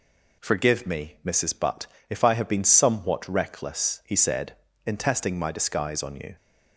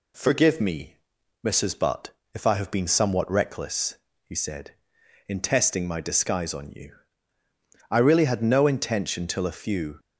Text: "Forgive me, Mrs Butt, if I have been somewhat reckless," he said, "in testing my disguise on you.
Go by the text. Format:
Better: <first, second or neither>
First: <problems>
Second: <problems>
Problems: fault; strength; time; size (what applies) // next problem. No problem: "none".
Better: first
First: none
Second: goes on to say "I really had no intention till a few"; strong; from 7.9 s on; 2.0 s long